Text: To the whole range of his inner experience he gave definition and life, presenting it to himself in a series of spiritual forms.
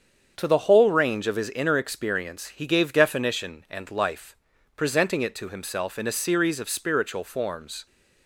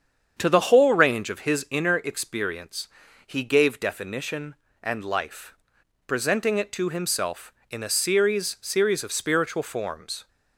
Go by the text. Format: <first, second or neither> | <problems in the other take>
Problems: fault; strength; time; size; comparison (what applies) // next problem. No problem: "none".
first | starts louder than the rest; strong; until 1.4 s; 7.5 dB; strong in the first // pauses between "experience" and "he"; at 2.8 s; 0.38 s long // says "series" twice; at 8.6 s